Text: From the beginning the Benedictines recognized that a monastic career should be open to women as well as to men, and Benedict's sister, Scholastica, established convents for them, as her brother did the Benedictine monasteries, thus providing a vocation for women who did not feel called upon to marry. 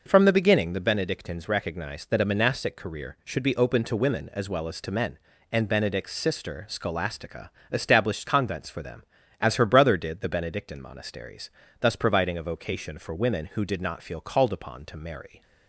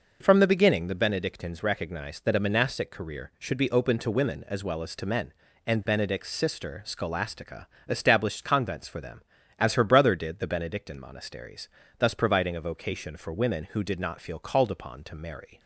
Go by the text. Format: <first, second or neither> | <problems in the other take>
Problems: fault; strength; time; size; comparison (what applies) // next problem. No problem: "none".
neither | none